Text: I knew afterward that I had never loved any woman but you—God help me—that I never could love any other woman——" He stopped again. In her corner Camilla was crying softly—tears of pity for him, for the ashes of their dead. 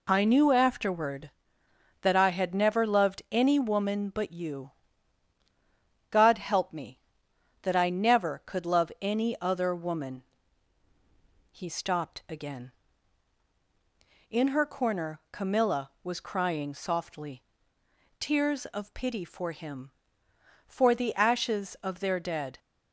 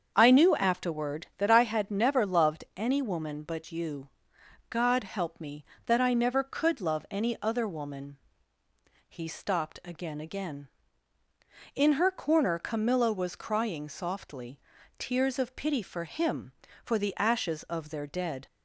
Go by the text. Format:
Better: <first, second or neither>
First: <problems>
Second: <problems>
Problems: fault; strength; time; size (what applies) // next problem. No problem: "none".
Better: first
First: none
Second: starts louder than the rest; until 1.1 s; 7 dB // says "again" twice; at 10.1 s